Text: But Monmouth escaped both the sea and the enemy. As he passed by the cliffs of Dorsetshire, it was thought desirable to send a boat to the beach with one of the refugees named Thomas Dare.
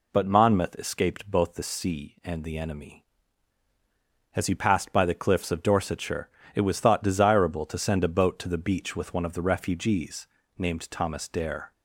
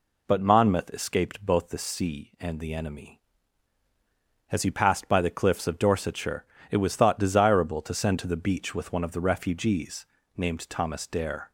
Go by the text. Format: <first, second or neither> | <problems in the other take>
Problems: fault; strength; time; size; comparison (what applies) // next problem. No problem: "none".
first | skips "a boat"; at 8.1 s // pauses between "refugees" and "named"; slight; at 10.0 s; 0.30 s long; slight in the first